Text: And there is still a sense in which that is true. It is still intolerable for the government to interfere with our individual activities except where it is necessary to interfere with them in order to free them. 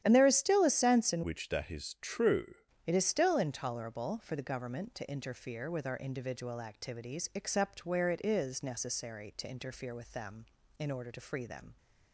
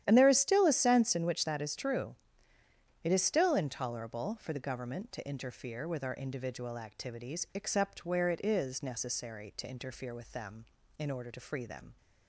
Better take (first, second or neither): second